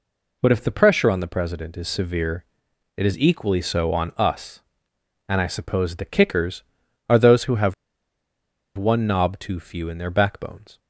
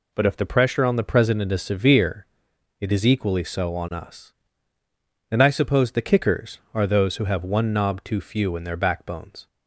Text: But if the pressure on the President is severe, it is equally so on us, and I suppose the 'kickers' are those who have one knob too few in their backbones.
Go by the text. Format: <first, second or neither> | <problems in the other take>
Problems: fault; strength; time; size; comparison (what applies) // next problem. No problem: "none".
second | pauses between "have" and "one"; at 7.7 s; 1.0 s long